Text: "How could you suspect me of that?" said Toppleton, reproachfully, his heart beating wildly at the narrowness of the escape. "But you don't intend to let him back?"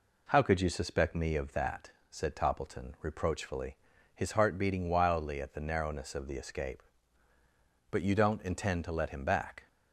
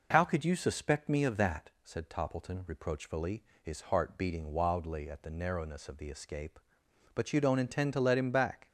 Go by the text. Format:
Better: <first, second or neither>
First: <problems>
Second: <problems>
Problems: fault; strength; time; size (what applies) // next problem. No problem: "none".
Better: neither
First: none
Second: none